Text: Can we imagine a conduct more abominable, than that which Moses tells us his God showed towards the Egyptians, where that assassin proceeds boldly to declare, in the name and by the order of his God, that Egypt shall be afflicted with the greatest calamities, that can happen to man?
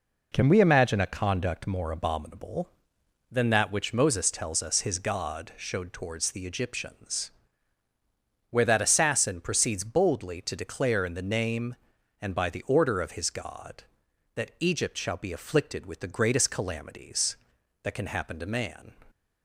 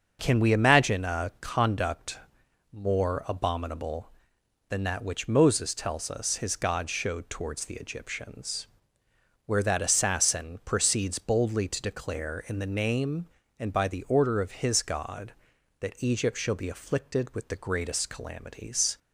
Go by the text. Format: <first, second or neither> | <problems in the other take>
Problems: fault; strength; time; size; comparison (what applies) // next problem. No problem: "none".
first | starts louder than the rest; until 1.2 s; 6.5 dB // pauses between "conduct" and "more"; noticeable; at 2.1 s; 0.56 s long // stops before "that can happen to man"; at 18.9 s